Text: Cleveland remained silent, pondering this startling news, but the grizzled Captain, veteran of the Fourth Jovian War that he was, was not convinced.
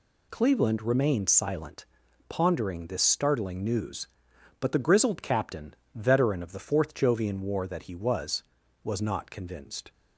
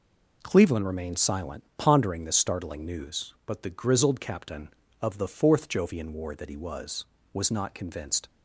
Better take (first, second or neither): first